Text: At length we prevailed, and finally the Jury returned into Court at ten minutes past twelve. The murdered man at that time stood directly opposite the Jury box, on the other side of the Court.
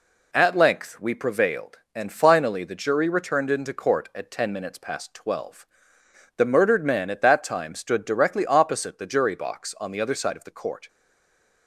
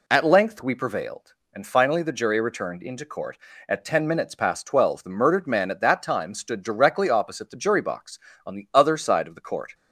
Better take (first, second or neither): second